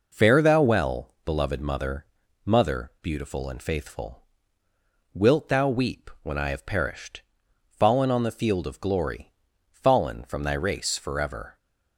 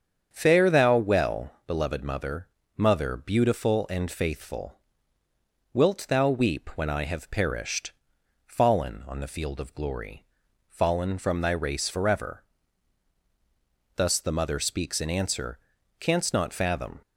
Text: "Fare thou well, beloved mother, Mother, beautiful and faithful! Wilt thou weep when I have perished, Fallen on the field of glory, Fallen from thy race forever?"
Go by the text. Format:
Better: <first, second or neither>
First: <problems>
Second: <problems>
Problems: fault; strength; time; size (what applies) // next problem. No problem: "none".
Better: first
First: none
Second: starts louder than the rest; strong; until 1.3 s; 7.5 dB // goes on to say "Thus the mother speaks in answer Canst not fathom"; strong; from 13.9 s on; 3.0 s long